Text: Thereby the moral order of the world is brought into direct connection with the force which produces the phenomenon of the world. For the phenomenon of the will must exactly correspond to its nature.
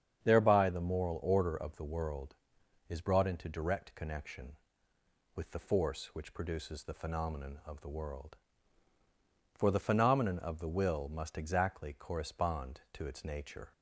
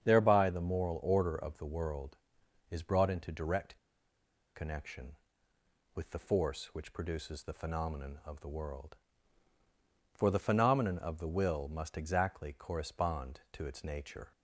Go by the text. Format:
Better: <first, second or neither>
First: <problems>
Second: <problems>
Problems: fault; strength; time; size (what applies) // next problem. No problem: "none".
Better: first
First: starts louder than the rest; strong; until 1.2 s; 8 dB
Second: starts louder than the rest; strong; until 1.0 s; 8 dB // pauses between "direct" and "connection"; noticeable; at 3.7 s; 0.78 s long